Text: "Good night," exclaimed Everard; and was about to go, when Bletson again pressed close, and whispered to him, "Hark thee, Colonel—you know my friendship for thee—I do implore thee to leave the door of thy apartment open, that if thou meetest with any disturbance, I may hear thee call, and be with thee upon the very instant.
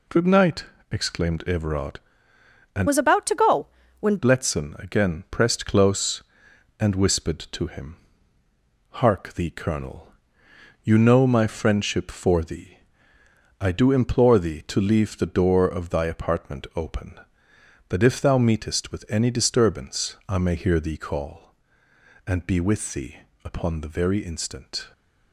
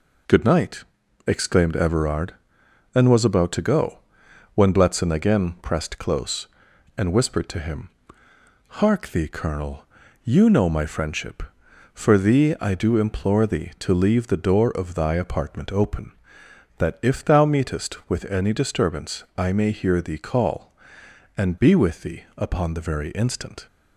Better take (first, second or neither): second